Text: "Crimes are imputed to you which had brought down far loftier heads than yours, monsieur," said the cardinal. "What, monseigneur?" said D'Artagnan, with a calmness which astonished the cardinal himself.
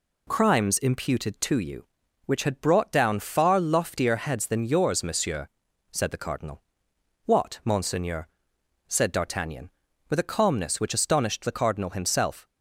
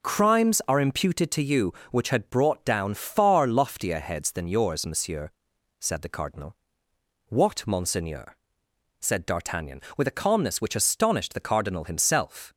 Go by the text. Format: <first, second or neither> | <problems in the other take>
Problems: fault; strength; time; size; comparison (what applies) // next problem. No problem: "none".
second | skips "are"; at 0.7 s